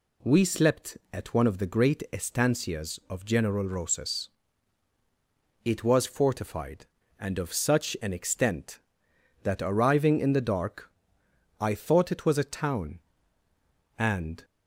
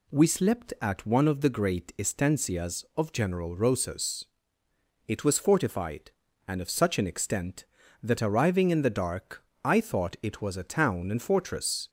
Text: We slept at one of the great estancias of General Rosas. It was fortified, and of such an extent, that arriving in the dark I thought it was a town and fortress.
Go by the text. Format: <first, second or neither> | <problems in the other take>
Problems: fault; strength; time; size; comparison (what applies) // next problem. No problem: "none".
second | pauses between "dark" and "I"; noticeable; at 10.8 s; 0.70 s long; slight in the second // stops before "fortress"; at 14.4 s